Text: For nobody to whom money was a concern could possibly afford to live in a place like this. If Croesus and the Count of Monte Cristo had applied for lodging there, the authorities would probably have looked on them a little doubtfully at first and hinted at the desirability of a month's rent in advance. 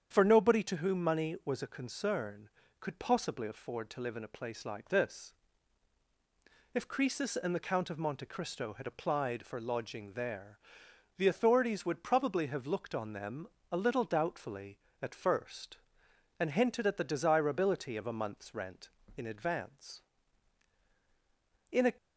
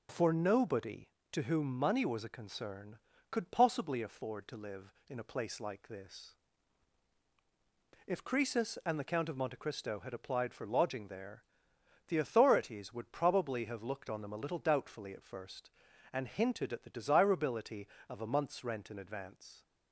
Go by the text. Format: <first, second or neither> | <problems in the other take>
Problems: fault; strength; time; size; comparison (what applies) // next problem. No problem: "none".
second | starts louder than the rest; strong; until 1.1 s; 8 dB // pauses between "them" and "a"; slight; at 13.4 s; 0.24 s long // goes on to say "In a"; slight; from 21.7 s on; 0.22 s long